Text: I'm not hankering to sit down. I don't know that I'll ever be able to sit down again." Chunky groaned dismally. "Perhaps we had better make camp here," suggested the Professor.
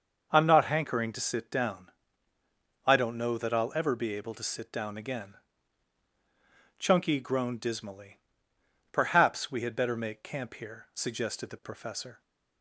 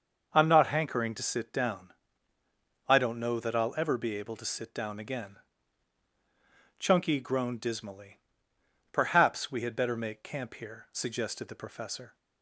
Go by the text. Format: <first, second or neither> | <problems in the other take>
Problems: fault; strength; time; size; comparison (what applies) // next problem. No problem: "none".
neither | starts louder than the rest; the same in both